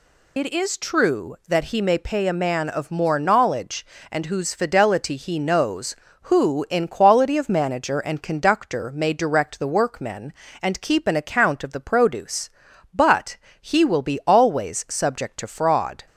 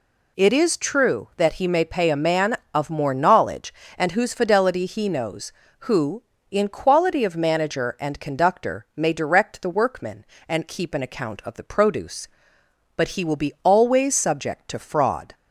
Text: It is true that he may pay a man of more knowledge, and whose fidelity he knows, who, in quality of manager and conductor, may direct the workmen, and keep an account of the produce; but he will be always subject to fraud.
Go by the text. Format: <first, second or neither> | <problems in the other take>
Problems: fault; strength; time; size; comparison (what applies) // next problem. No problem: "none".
second | loses the start of "It"; at 0.3 s; 45 ms // pauses between "but" and "he"; slight; at 13.3 s; 0.26 s long